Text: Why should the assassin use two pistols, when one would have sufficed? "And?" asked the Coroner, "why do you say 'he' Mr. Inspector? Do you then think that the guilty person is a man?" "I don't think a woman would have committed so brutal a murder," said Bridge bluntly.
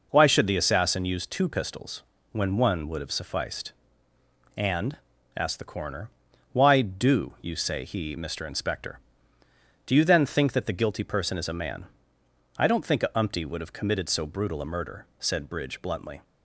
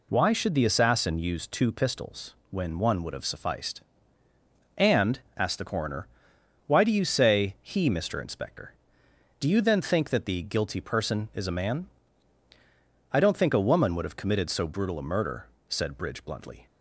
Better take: second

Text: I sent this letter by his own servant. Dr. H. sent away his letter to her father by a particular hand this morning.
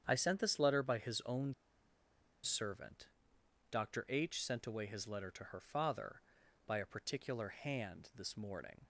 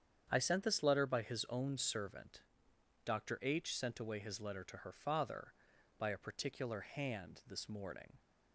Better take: second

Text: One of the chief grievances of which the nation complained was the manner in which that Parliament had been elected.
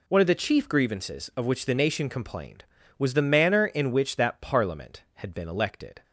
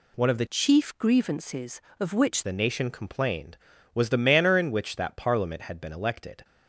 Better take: first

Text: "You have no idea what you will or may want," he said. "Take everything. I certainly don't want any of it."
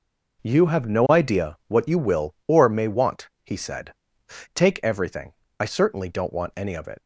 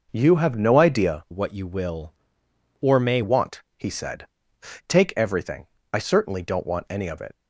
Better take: first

